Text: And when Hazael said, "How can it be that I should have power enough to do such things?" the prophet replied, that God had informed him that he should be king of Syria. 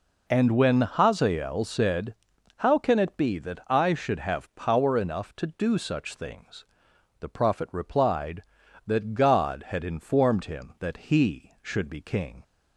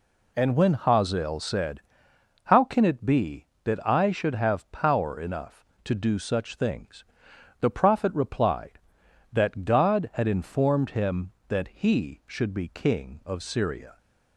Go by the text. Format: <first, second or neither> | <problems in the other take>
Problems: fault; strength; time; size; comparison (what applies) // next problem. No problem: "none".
second | stops before "of Syria"; at 12.4 s